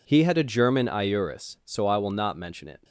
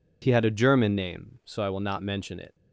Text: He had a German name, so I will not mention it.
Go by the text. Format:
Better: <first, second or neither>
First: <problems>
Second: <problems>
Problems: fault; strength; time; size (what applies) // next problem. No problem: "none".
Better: second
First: says "iuris" for "name"; at 0.8 s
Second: none